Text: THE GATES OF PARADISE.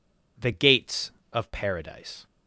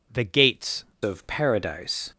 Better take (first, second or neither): first